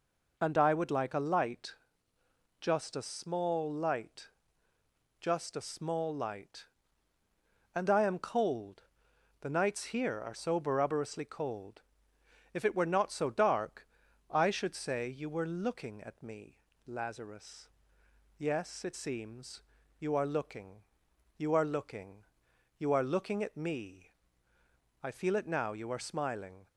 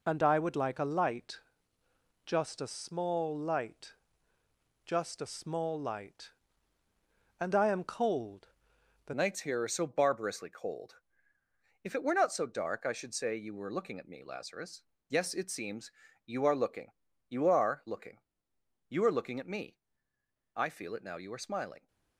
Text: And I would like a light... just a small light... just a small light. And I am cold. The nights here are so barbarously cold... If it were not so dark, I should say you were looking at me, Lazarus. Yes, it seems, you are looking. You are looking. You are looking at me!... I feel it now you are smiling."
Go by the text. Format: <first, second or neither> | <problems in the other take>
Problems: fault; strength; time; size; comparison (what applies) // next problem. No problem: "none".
first | changes voice at "nights"; from 9.1 s on; 12.7 s long